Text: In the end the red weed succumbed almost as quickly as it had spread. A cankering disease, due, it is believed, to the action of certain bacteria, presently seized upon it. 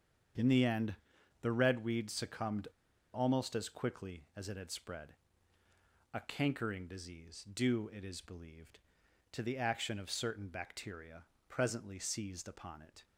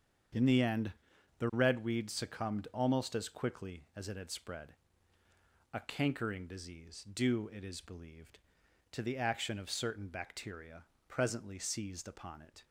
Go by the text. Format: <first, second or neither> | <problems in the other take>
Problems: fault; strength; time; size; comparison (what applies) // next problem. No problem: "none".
second | starts louder than the rest; strong; until 1.8 s; 7.5 dB; strong in the second // pauses between "end" and "the"; noticeable; at 0.9 s; 0.46 s long; noticeable in the second // pauses between "succumbed" and "almost"; noticeable; at 2.6 s; 0.46 s long